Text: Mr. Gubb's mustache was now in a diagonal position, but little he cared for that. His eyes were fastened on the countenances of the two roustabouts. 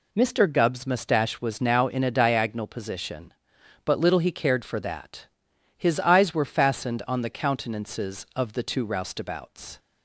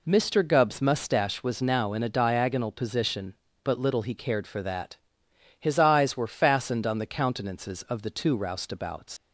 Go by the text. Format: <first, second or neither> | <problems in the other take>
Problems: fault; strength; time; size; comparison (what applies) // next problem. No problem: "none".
first | leaves "roustabouts" unfinished; at 9.1 s; 125 ms